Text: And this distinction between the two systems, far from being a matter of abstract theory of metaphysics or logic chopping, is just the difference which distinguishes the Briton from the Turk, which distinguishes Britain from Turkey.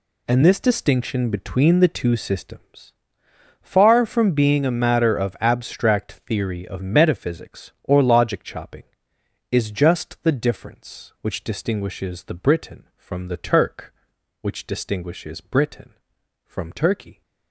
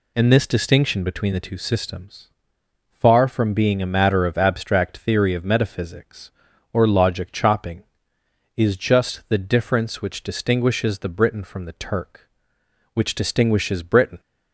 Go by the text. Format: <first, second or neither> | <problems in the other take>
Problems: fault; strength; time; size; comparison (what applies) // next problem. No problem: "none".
first | stops before "from Turkey"; at 14.1 s